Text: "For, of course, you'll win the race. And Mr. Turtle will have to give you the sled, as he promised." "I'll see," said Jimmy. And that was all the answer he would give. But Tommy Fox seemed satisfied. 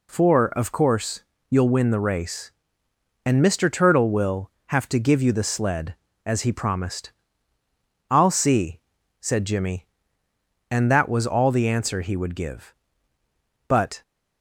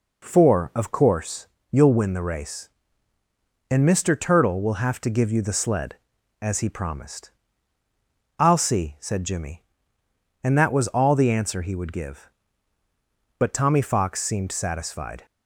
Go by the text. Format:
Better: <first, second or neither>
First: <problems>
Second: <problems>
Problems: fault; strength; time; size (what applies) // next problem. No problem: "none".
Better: second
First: stops before "Tommy Fox seemed satisfied"; at 14.0 s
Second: none